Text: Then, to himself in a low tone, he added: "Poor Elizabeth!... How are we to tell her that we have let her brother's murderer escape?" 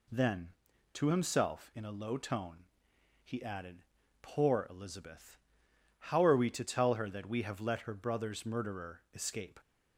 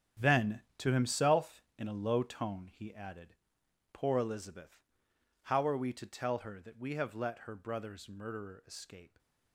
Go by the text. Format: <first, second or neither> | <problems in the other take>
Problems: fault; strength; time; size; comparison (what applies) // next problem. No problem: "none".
first | gets quieter; strong; throughout; 11 dB